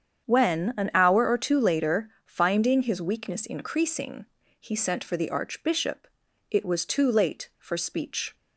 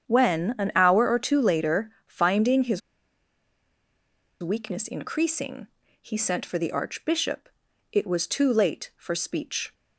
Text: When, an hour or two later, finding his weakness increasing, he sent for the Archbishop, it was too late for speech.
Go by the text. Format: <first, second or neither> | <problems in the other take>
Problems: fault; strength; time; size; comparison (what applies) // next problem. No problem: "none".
first | starts louder than the rest; strong; until 1.1 s; 8.5 dB; strong in the first // pauses between "his" and "weakness"; strong; at 2.8 s; 1.6 s long